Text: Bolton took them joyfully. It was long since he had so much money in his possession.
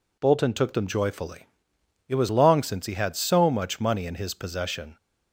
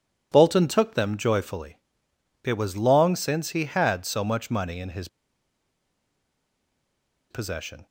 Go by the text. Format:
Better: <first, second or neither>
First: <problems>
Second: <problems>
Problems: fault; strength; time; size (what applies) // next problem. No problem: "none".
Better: first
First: none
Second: pauses between "his" and "possession"; strong; at 5.0 s; 2.2 s long